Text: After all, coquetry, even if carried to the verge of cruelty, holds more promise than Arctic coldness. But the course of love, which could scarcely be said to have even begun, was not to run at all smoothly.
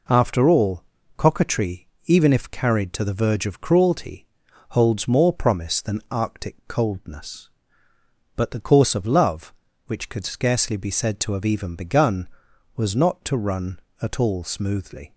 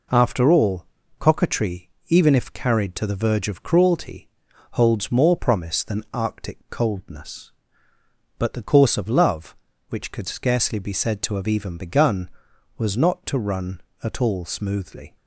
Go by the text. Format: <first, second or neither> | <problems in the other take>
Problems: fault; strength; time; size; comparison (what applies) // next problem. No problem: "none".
neither | none